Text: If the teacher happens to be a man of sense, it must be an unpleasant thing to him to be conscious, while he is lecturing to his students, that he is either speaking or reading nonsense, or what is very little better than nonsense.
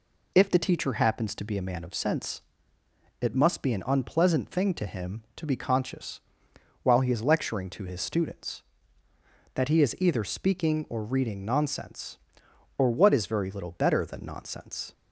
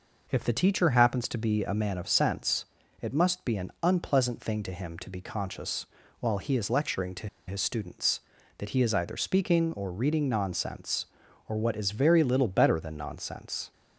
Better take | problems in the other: first | pauses between "to" and "his"; slight; at 7.2 s; 0.20 s long

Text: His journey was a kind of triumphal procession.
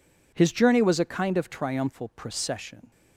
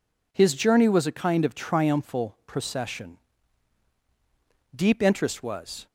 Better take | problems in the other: first | goes on to say "Deep interest was"; noticeable; from 4.7 s on; 1.1 s long

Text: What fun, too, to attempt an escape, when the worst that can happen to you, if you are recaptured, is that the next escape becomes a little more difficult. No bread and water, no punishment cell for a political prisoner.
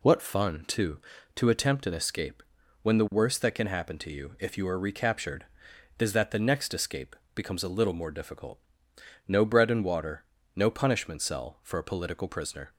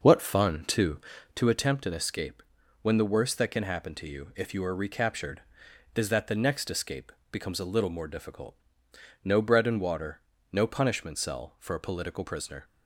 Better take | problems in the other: first | starts louder than the rest; noticeable; until 1.5 s; 6 dB // pauses between "escape" and "becomes"; slight; at 7.1 s; 0.18 s long; slight in the first

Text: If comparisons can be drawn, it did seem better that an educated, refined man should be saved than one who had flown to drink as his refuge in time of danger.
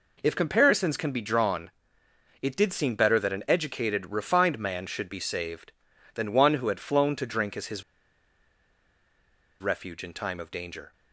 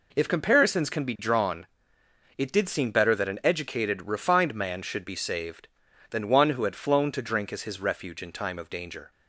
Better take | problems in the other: second | pauses between "his" and "refuge"; strong; at 7.8 s; 1.7 s long

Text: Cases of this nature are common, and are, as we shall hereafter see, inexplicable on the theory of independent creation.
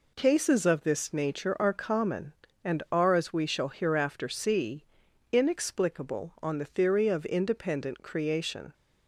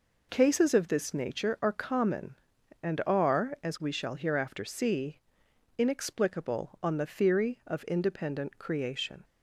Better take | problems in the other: neither | none

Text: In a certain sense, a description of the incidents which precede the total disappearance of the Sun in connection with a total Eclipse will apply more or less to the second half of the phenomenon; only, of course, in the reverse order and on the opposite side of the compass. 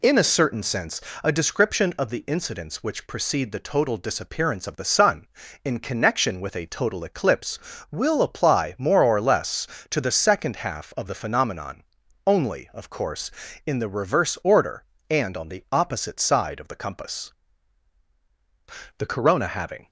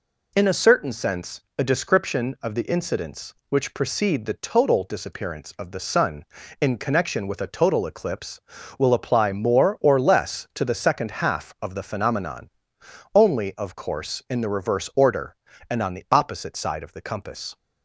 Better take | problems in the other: second | goes on to say "The Corona having"; noticeable; from 18.9 s on; 0.90 s long

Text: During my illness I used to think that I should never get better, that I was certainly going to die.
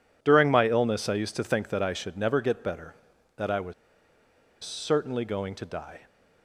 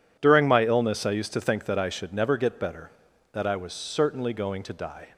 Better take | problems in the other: second | pauses between "was" and "certainly"; noticeable; at 3.7 s; 0.90 s long

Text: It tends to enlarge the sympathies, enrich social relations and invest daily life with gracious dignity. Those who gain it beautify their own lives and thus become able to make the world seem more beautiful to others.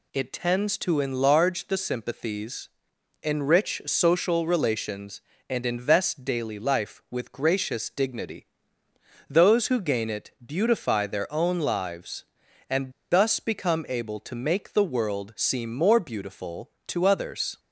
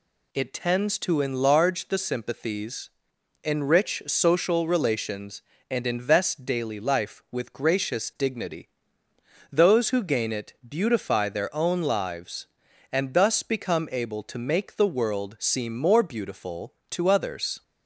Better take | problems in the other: second | pauses between "and" and "thus"; slight; at 12.9 s; 0.19 s long

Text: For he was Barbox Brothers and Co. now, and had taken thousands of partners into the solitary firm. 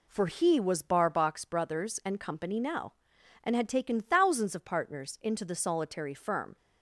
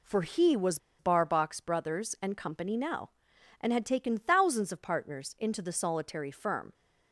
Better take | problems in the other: first | pauses between "was" and "Barbox"; slight; at 0.7 s; 0.20 s long

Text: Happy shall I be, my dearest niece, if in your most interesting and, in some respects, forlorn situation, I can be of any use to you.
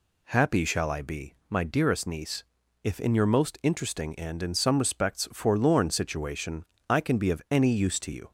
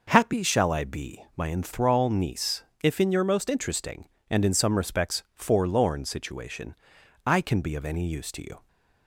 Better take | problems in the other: first | says "enthrall" for "dearest"; at 1.4 s

